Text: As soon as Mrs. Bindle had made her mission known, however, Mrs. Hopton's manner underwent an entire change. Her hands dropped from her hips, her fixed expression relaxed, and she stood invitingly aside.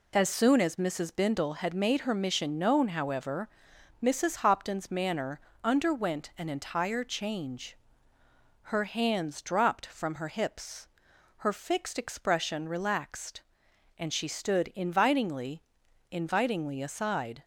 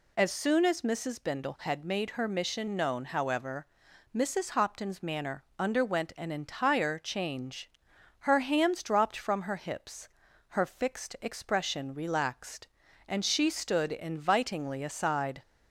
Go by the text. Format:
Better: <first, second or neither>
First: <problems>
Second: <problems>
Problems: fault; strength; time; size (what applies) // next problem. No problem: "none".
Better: second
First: pauses between "manner" and "underwent"; slight; at 5.4 s; 0.20 s long // says "invitingly" twice; at 16.0 s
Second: none